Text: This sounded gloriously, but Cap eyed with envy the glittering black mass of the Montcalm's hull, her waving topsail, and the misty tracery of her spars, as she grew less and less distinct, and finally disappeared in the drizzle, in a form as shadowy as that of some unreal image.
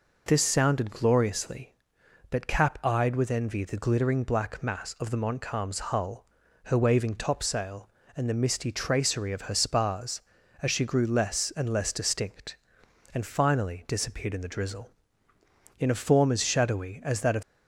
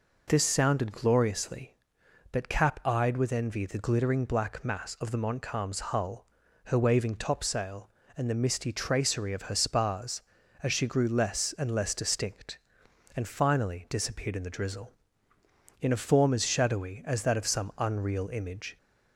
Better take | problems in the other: second | stops before "some unreal image"; at 17.4 s

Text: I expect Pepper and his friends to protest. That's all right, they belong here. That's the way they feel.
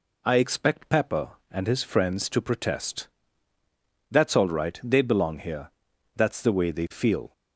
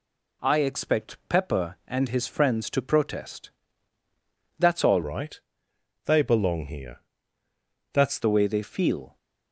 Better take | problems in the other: first | changes voice from "right" to "That's"; from 5.0 to 8.1 s; 3.1 s long

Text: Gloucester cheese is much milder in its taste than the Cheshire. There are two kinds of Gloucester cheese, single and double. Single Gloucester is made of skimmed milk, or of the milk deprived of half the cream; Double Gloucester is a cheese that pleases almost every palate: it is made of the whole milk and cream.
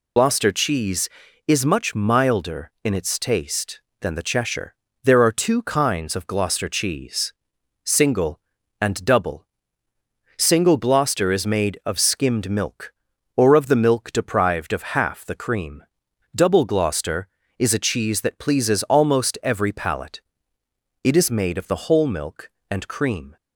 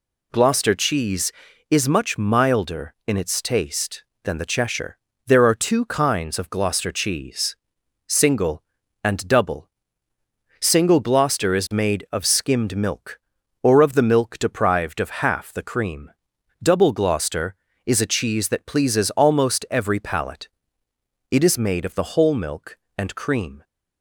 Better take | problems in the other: second | loses the start of "Gloucester"; at 0.1 s; 75 ms

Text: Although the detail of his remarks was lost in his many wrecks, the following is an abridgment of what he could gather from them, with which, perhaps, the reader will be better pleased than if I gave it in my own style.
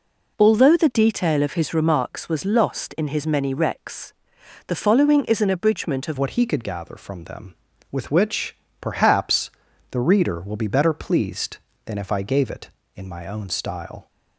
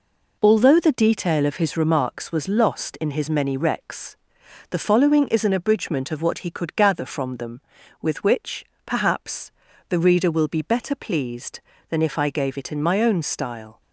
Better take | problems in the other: second | changes voice at "what"; from 6.1 s on; 7.9 s long

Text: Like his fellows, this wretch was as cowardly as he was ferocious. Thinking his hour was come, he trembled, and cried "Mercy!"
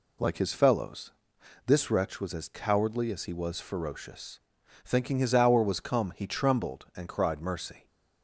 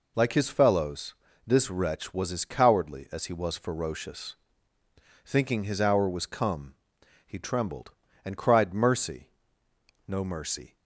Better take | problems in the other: first | goes on to say "No mercy"; noticeable; from 10.0 s on; 0.72 s long

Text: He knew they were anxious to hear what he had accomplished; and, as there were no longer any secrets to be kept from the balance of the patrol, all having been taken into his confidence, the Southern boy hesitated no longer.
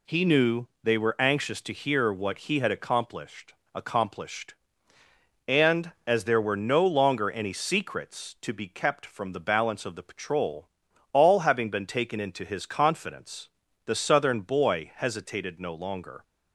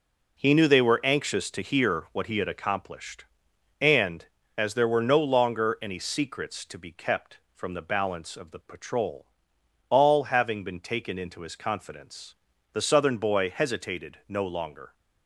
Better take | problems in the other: second | pauses between "knew" and "they"; slight; at 0.6 s; 0.16 s long // says "accomplished" twice; at 3.7 s

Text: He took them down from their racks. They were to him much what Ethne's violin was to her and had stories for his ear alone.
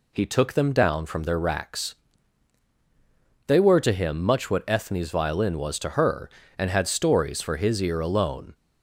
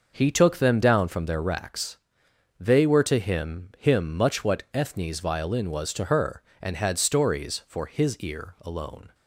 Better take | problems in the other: first | says "him" twice; at 3.7 s

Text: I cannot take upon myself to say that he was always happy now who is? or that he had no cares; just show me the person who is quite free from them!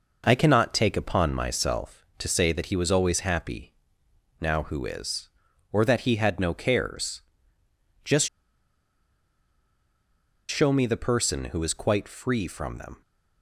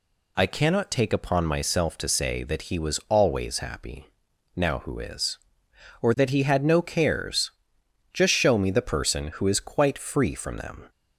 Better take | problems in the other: second | pauses between "happy" and "now"; noticeable; at 3.7 s; 0.66 s long; noticeable in the second // pauses between "just" and "show"; strong; at 8.2 s; 2.2 s long

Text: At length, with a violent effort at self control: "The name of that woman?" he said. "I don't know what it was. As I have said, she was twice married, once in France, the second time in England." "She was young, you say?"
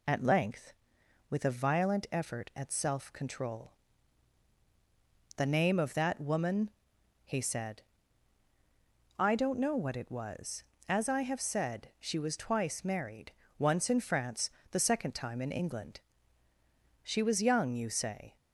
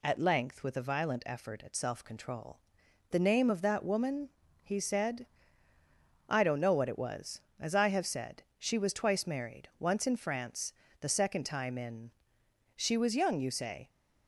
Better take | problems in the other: first | skips "England"; at 12.4 s

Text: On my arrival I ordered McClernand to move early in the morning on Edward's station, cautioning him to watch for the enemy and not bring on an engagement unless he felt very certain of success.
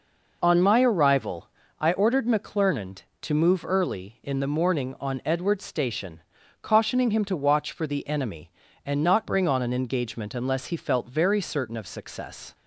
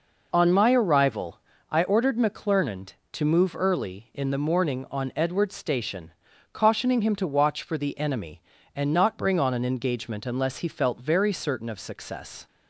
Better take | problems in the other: neither | pauses between "arrival" and "I"; slight; the same in both

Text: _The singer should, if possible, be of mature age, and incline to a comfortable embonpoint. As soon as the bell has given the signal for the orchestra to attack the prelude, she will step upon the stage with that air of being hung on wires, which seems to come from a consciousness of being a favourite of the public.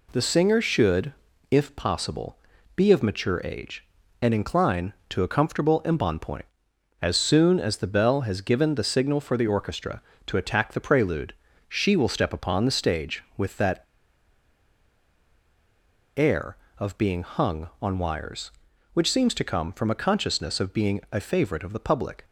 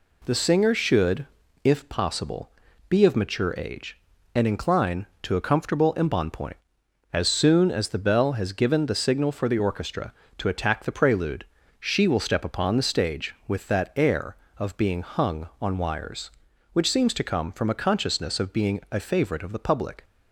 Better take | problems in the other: second | pauses between "that" and "air"; strong; at 13.8 s; 2.3 s long

